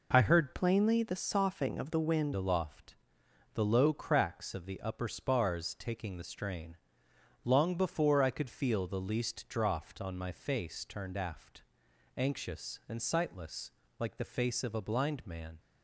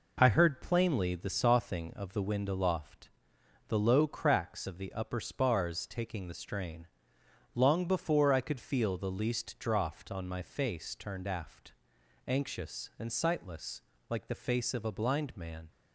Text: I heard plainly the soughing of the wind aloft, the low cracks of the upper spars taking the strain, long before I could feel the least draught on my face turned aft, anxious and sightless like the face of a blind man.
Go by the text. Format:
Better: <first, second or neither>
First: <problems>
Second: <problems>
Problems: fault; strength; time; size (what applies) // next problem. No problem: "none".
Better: second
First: changes voice from "plainly" to "wind"; from 0.5 to 2.3 s; 1.8 s long // pauses between "sightless" and "like"; slight; at 13.7 s; 0.28 s long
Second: pauses between "sightless" and "like"; slight; at 13.8 s; 0.28 s long